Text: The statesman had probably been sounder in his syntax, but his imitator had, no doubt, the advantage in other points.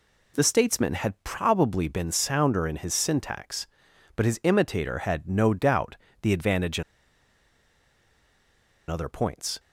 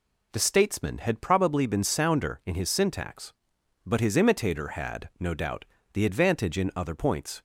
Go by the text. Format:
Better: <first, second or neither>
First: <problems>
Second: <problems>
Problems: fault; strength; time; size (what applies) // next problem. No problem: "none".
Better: second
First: pauses between "in" and "other"; strong; at 6.8 s; 2.0 s long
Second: none